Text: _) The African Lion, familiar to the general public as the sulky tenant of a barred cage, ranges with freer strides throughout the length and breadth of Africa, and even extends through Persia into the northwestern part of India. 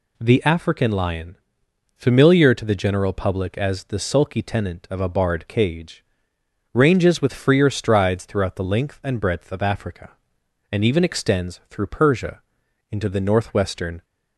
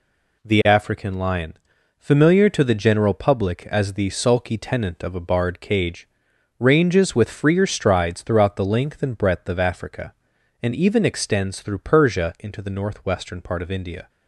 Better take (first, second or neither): second